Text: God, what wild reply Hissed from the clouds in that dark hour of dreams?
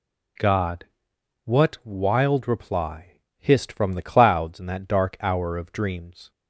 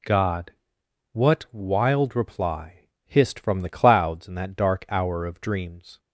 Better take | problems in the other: neither | pauses between "reply" and "Hissed"; slight; the same in both

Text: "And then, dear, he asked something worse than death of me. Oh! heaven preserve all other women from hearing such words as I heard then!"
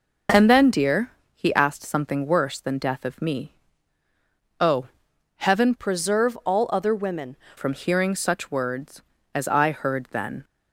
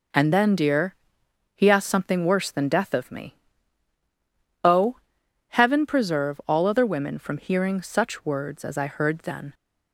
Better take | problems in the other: second | changes voice from "preserve" to "women"; from 5.7 to 7.3 s; 1.6 s long

